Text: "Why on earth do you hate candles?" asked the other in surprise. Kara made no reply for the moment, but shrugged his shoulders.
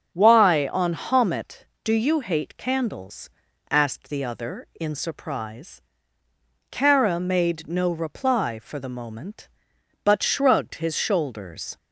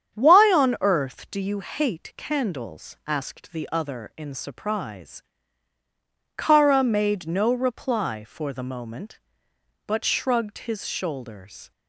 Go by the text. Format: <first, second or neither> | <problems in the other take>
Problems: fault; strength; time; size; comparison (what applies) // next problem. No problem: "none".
second | starts louder than the rest; strong; until 1.1 s; 7.5 dB; strong in the second // says "homet" for "earth"; at 0.9 s